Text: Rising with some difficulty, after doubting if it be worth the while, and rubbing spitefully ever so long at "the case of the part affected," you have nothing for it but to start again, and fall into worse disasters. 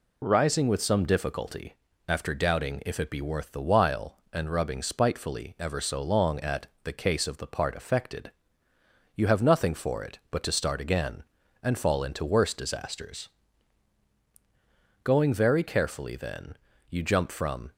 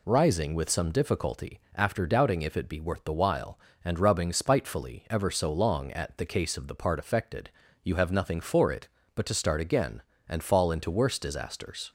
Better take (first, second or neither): second